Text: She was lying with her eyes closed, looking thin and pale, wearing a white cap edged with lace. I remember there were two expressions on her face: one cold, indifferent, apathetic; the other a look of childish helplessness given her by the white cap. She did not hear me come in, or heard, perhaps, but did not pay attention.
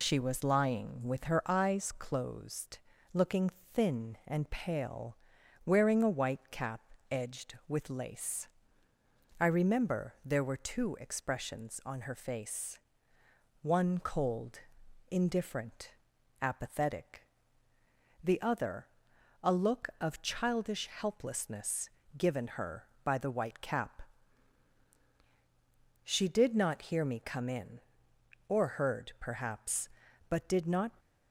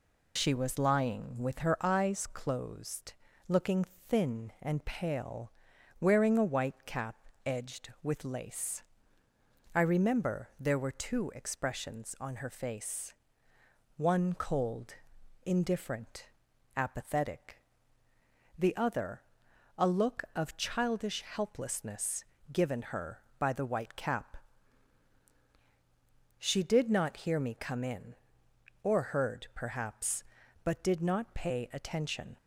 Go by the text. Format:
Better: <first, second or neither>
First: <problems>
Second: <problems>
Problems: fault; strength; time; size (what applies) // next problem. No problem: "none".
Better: second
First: pauses between "looking" and "thin"; slight; at 3.5 s; 0.20 s long // pauses between "cap" and "edged"; slight; at 6.7 s; 0.32 s long // pauses between "other" and "a"; noticeable; at 18.8 s; 0.56 s long // pauses between "helplessness" and "given"; slight; at 21.8 s; 0.28 s long // stops before "pay attention"; at 30.9 s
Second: pauses between "looking" and "thin"; slight; at 3.8 s; 0.20 s long // pauses between "cap" and "edged"; slight; at 7.1 s; 0.32 s long // pauses between "other" and "a"; noticeable; at 19.2 s; 0.56 s long // pauses between "helplessness" and "given"; slight; at 22.2 s; 0.28 s long